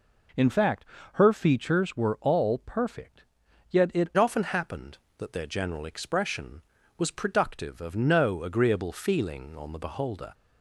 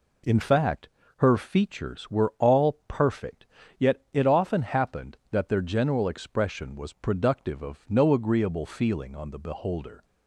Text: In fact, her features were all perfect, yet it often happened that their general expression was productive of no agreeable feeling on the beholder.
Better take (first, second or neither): second